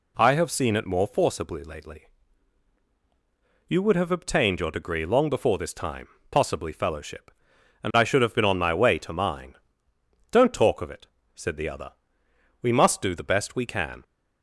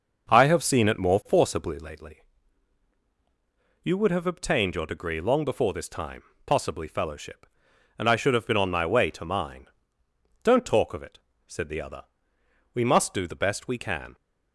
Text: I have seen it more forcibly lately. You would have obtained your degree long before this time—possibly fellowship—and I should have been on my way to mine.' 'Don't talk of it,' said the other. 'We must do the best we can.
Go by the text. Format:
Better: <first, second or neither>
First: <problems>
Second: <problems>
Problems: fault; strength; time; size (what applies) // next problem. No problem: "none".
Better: first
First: none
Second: starts louder than the rest; noticeable; until 2.0 s; 6 dB